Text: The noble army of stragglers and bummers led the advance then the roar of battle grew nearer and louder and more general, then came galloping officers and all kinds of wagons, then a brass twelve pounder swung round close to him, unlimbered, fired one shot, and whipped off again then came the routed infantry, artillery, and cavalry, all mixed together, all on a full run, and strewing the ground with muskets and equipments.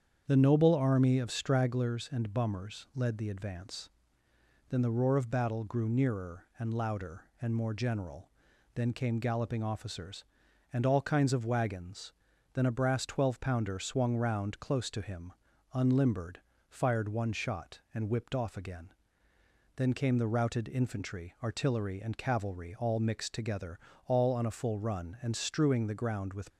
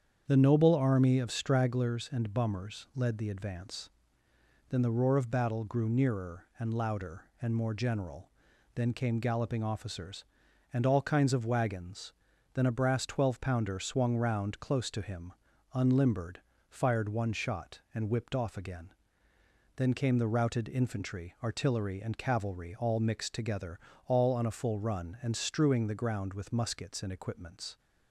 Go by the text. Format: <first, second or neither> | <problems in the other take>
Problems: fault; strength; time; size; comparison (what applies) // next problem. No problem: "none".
second | starts louder than the rest; strong; until 1.2 s; 8 dB; strong in the second // pauses between "advance" and "then"; noticeable; at 3.8 s; 0.80 s long; noticeable in the second // pauses between "again" and "then"; noticeable; at 18.9 s; 0.86 s long; noticeable in the second // stops before "muskets and equipments"; at 26.5 s